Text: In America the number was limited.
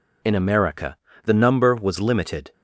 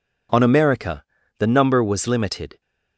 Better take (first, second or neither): first